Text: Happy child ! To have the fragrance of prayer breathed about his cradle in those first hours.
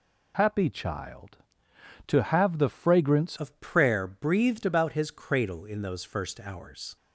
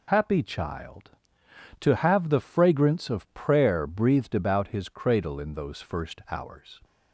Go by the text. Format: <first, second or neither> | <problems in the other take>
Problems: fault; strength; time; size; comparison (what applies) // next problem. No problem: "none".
second | changes voice at "of"; from 3.3 s on; 3.6 s long